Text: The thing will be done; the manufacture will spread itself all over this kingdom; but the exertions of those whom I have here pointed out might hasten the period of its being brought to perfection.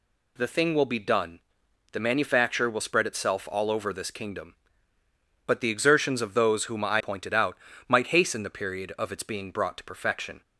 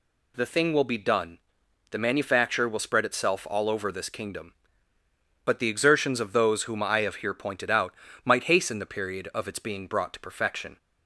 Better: second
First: skips "have here"; at 7.0 s // pauses between "out" and "might"; slight; at 7.5 s; 0.30 s long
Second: pauses between "out" and "might"; slight; at 7.9 s; 0.30 s long

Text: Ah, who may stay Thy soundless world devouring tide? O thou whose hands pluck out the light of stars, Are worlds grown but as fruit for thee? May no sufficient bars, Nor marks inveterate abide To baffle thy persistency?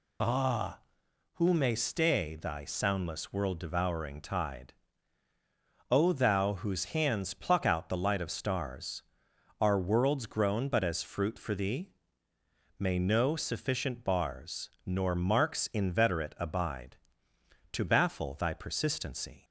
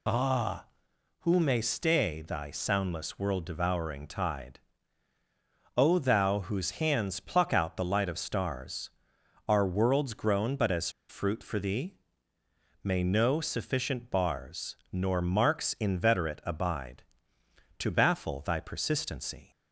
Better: first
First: none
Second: pauses between "as" and "fruit"; slight; at 10.8 s; 0.19 s long

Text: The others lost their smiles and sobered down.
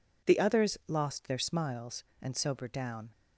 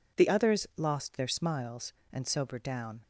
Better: neither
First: none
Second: none

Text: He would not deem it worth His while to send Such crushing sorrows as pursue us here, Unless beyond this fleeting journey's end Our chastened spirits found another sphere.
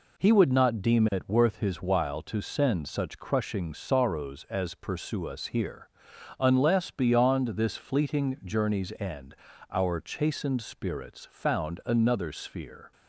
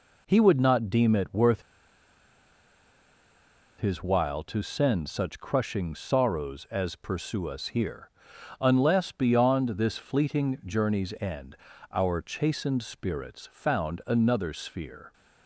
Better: first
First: pauses between "end" and "Our"; at 9.3 s; 0.38 s long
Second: pauses between "worth" and "His"; strong; at 1.6 s; 2.1 s long // pauses between "end" and "Our"; at 11.5 s; 0.38 s long

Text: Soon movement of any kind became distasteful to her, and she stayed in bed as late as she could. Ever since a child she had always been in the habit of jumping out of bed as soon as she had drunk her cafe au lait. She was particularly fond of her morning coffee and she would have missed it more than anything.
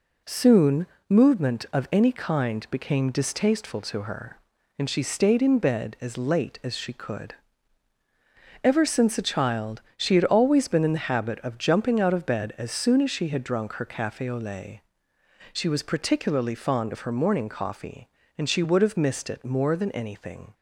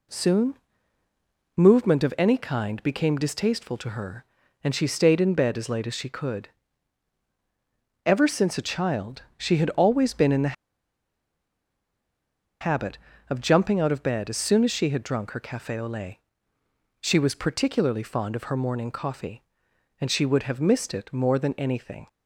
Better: first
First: pauses between "Soon" and "movement"; slight; at 0.8 s; 0.24 s long // pauses between "child" and "she"; slight; at 9.8 s; 0.16 s long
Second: pauses between "Soon" and "movement"; at 0.5 s; 1.0 s long // pauses between "child" and "she"; slight; at 9.2 s; 0.16 s long // pauses between "the" and "habit"; strong; at 10.5 s; 2.0 s long

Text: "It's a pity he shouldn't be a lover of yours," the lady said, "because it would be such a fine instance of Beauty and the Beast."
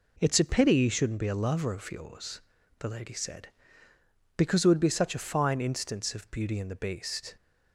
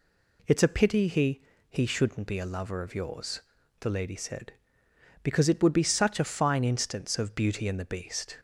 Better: first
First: none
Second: says "he" twice; at 1.6 s

